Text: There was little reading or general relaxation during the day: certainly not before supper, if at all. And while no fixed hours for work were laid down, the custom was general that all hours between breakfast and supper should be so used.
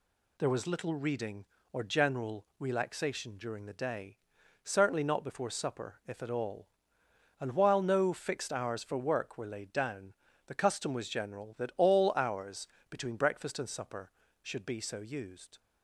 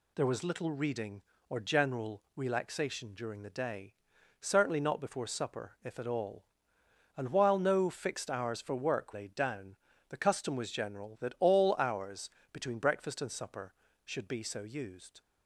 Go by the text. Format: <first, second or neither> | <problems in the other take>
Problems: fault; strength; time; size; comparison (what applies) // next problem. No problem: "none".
first | skips "were"; at 9.1 s // pauses between "hours" and "between"; slight; at 12.2 s; 0.22 s long; slight in the first